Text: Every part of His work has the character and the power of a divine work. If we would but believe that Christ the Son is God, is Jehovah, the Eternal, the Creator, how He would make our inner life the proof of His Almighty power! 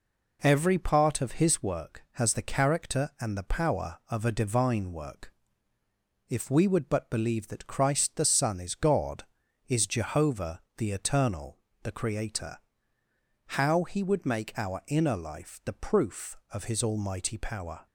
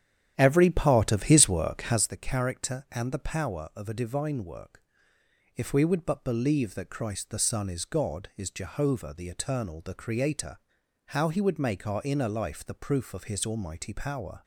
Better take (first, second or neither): first